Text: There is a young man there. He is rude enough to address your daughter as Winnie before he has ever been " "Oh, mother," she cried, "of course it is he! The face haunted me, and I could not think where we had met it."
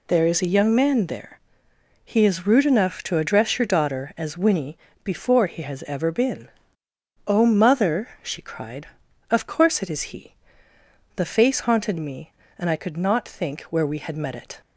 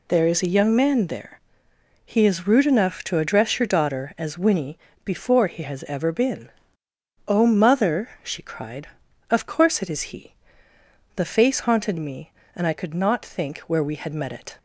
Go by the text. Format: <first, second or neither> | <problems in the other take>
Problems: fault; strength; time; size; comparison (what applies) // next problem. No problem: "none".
neither | pauses between "Winnie" and "before"; slight; the same in both